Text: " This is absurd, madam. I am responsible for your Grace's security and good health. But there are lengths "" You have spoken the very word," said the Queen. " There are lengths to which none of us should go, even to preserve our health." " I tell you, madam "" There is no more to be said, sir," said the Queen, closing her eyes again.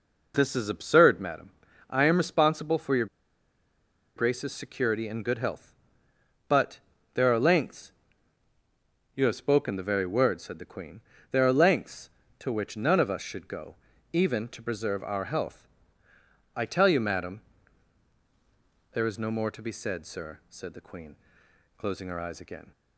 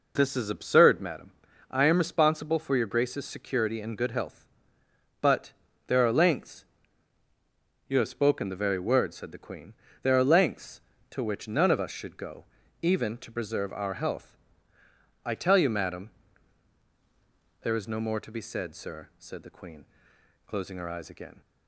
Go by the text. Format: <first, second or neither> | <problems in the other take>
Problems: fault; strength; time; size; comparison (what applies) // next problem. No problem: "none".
second | pauses between "your" and "Grace's"; at 3.0 s; 1.1 s long // pauses between "But" and "there"; slight; at 6.7 s; 0.36 s long; slight in the second